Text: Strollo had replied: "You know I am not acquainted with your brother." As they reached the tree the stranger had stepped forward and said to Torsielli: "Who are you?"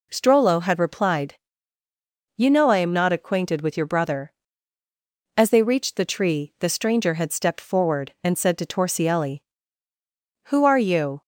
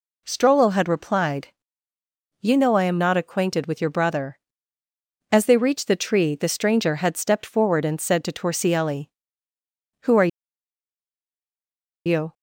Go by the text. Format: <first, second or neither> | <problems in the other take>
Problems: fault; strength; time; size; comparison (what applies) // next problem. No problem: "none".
first | pauses between "are" and "you"; strong; at 10.2 s; 1.7 s long